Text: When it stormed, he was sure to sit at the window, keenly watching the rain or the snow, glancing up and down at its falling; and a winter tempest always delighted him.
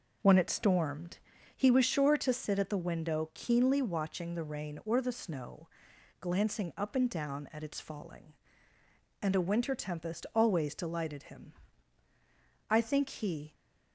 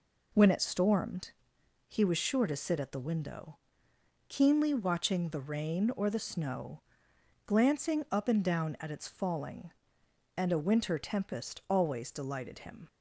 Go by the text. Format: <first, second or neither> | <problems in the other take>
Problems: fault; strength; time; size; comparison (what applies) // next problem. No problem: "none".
second | goes on to say "I think he"; noticeable; from 12.6 s on; 0.84 s long